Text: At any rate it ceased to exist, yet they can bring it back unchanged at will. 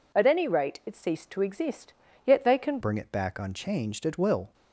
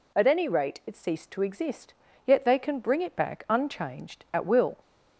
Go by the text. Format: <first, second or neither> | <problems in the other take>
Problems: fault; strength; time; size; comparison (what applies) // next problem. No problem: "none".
second | changes voice at "bring"; from 2.8 s on; 1.7 s long